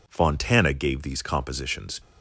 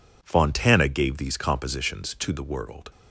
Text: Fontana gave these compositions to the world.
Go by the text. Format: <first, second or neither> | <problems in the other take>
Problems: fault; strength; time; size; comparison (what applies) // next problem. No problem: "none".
second | stops before "to the world"; at 1.9 s